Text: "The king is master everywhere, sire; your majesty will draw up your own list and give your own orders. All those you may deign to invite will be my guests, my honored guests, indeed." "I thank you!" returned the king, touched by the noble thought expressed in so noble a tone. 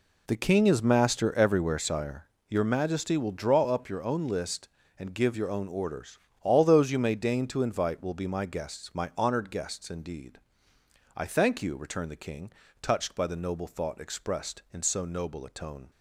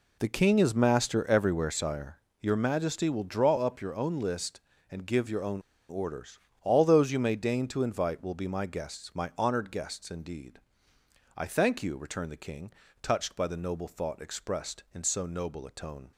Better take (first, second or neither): first